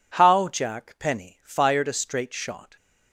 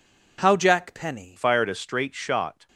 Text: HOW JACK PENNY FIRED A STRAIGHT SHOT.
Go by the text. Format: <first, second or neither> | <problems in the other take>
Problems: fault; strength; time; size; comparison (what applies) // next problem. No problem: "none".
first | changes voice at "FIRED"; from 1.3 s on; 1.3 s long